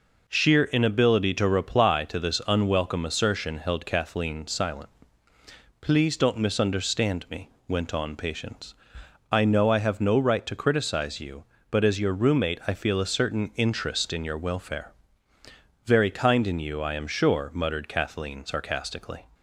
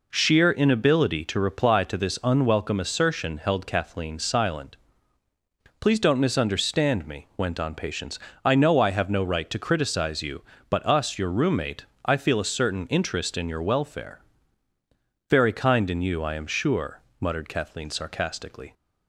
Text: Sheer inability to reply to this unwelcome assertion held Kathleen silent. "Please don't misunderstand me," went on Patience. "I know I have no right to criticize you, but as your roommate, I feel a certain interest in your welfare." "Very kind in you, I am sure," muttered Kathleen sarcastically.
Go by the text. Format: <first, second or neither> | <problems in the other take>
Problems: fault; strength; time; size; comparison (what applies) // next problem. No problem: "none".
first | says "us" for "as"; at 10.8 s